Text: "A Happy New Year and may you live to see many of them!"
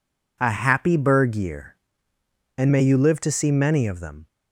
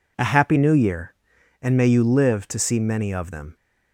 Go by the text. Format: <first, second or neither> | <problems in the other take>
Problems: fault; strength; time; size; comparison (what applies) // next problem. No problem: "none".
second | says "Berg" for "New"; at 0.9 s